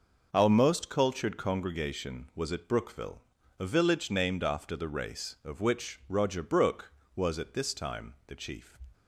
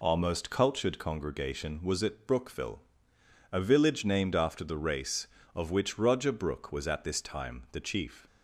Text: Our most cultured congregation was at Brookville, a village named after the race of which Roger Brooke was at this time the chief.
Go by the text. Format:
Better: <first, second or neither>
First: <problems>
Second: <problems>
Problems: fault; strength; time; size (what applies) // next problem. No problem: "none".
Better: neither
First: none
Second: none